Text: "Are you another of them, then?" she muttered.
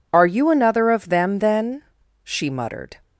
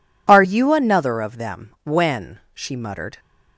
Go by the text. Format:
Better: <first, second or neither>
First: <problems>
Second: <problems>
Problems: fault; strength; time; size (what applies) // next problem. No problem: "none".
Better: first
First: none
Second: says "when" for "then"; at 1.8 s